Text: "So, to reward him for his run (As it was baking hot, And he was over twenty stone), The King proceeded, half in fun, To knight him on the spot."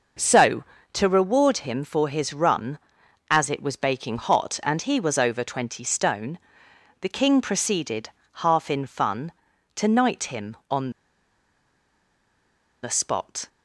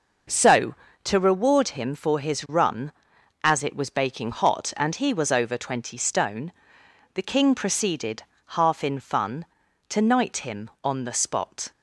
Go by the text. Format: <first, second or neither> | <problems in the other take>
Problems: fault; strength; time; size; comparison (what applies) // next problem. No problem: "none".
second | pauses between "on" and "the"; strong; at 10.8 s; 1.9 s long